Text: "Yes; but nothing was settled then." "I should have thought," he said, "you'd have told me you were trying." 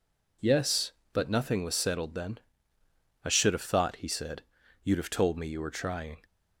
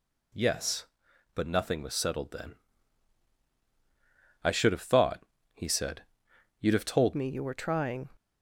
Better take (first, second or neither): first